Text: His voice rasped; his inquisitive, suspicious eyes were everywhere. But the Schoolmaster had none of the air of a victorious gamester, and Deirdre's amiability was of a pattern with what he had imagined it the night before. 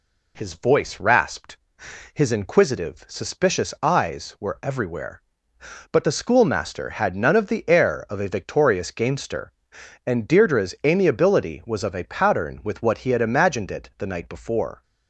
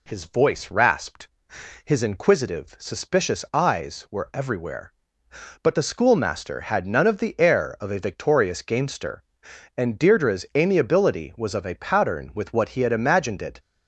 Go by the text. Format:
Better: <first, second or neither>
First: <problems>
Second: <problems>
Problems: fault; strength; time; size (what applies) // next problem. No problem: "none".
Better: first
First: none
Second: stops before "the night before"; at 13.5 s